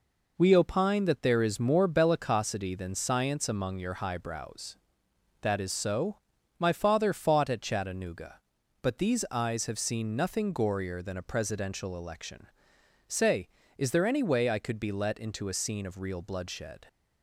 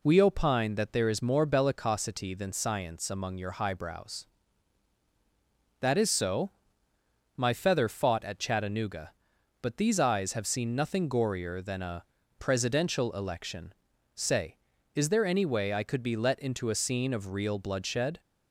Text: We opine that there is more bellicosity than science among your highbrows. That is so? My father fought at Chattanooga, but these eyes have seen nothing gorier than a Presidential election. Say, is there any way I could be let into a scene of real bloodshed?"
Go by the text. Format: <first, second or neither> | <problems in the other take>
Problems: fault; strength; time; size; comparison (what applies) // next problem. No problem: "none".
first | says "feather" for "father"; at 7.5 s // pauses between "a" and "Presidential"; slight; at 12.0 s; 0.36 s long